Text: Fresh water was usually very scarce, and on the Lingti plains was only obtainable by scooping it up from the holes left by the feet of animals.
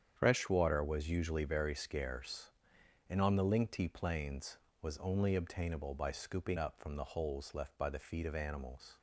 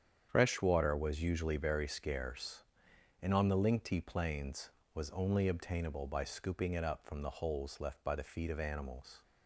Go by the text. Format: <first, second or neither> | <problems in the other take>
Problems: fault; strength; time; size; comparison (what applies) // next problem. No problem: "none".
second | starts louder than the rest; strong; until 1.1 s; 8.5 dB; strong in the second // skips "it"; at 6.5 s